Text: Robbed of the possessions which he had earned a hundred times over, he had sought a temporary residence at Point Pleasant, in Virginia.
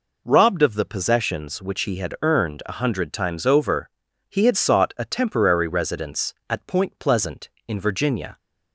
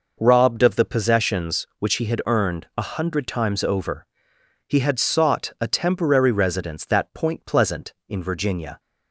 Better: first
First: none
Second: says "that" for "at"; at 6.8 s

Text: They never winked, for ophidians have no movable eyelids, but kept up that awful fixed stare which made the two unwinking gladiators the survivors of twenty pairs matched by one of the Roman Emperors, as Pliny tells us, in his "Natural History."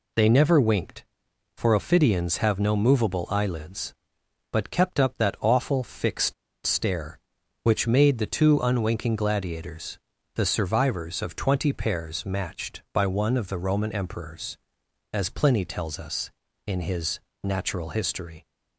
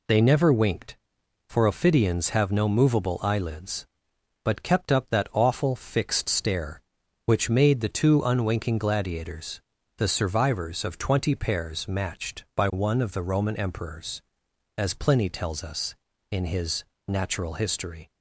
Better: second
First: pauses between "fixed" and "stare"; slight; at 6.3 s; 0.31 s long // pauses between "gladiators" and "the"; slight; at 9.9 s; 0.36 s long // pauses between "his" and "Natural"; slight; at 17.1 s; 0.24 s long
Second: pauses between "gladiators" and "the"; slight; at 9.6 s; 0.36 s long // pauses between "his" and "Natural"; slight; at 16.8 s; 0.24 s long

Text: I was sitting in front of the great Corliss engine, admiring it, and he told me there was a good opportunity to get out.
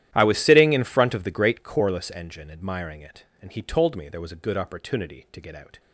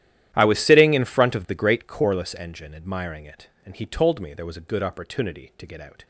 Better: neither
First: starts louder than the rest; strong; until 1.1 s; 12.5 dB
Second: starts louder than the rest; strong; until 1.3 s; 12.5 dB

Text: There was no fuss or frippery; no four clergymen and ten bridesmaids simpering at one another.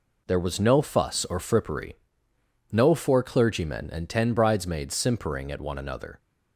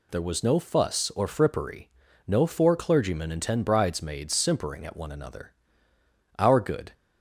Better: first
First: none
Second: goes on to say "Our good"; from 6.3 s on; 0.54 s long

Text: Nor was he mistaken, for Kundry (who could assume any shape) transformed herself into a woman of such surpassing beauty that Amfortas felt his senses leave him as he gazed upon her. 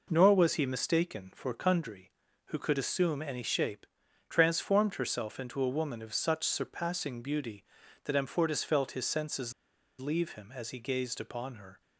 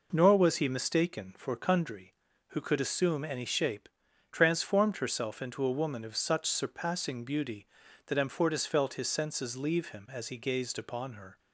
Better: second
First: pauses between "senses" and "leave"; noticeable; at 9.5 s; 0.45 s long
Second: none

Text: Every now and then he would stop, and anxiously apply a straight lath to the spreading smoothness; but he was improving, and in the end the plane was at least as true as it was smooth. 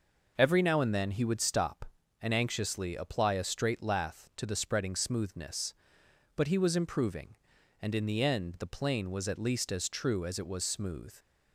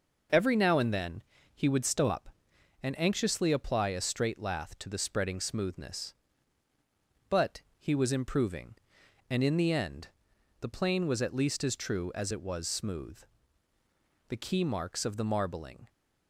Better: first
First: none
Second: pauses between "then" and "he"; slight; at 1.2 s; 0.30 s long // pauses between "end" and "the"; noticeable; at 10.0 s; 0.54 s long // goes on to say "The key marks of the marbling"; from 14.2 s on; 1.6 s long

